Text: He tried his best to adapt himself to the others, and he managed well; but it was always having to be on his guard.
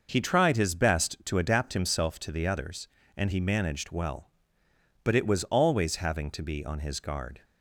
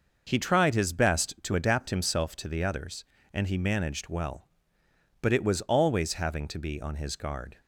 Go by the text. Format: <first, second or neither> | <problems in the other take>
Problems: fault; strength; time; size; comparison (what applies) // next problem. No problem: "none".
neither | none